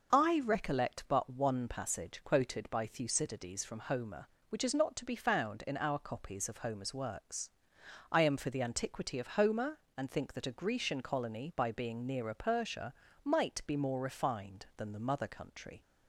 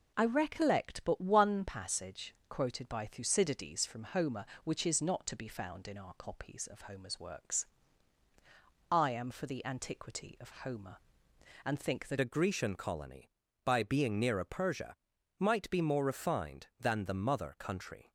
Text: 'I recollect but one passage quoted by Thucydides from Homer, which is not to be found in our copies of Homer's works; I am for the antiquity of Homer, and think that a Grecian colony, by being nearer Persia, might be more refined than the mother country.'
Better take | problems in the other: first | changes voice at "a"; from 12.2 s on; 5.9 s long

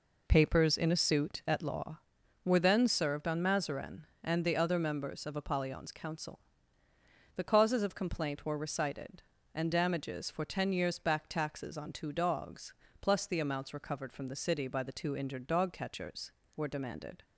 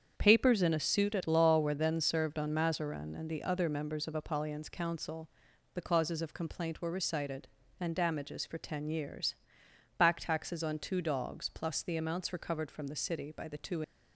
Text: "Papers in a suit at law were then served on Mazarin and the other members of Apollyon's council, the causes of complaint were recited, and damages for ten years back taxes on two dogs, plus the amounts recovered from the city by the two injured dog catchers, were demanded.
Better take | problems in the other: first | starts louder than the rest; strong; until 1.1 s; 7.5 dB // pauses between "years" and "back"; noticeable; at 9.3 s; 0.64 s long // stops before "injured dog catchers were demanded"; at 13.8 s

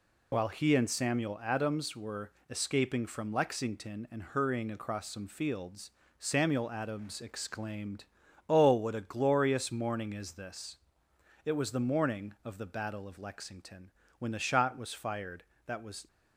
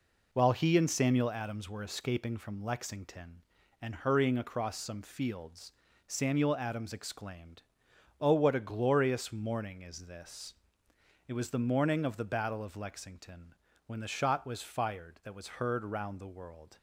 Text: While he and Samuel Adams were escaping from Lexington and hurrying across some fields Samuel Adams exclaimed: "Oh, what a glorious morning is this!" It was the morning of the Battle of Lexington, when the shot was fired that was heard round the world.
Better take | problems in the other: second | pauses between "were" and "escaping"; slight; at 2.3 s; 0.18 s long // pauses between "fields" and "Samuel"; slight; at 5.9 s; 0.26 s long; slight in the second // stops before "heard round the world"; at 16.0 s

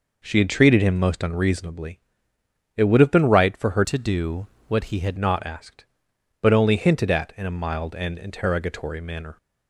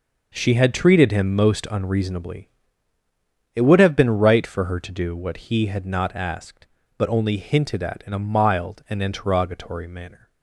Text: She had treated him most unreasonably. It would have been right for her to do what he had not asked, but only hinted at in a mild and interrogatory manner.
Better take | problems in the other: second | changes voice from "to" to "had"; from 3.8 to 5.1 s; 1.3 s long // pauses between "do" and "what"; slight; at 4.4 s; 0.22 s long

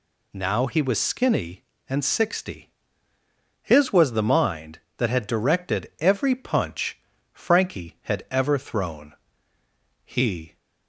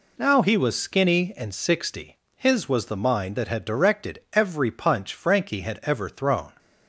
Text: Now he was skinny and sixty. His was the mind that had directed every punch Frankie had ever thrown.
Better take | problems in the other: second | pauses between "punch" and "Frankie"; slight; at 6.9 s; 0.32 s long // goes on to say "He"; from 10.0 s on; 0.54 s long

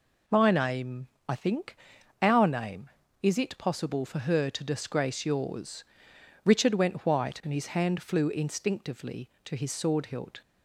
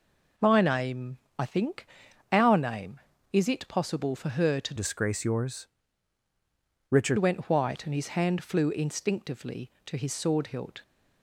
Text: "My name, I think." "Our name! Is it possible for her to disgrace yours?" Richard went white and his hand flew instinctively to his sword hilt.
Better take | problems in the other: first | changes voice from "disgrace" to "Richard"; from 4.7 to 7.1 s; 2.4 s long

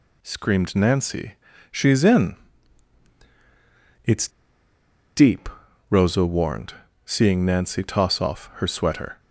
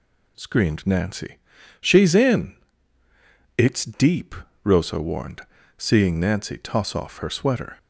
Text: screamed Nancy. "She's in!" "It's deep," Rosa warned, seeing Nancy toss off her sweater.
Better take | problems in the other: second | pauses between "It's" and "deep"; noticeable; at 4.2 s; 0.87 s long

